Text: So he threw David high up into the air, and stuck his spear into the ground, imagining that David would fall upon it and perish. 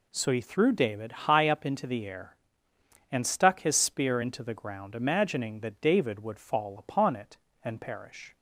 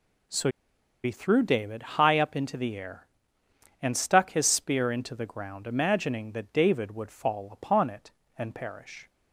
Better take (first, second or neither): first